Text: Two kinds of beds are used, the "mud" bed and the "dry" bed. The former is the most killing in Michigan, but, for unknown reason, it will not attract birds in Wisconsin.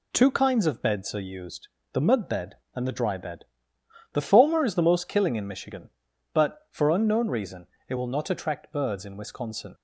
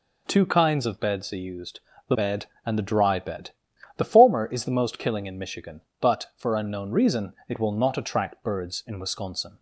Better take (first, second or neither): first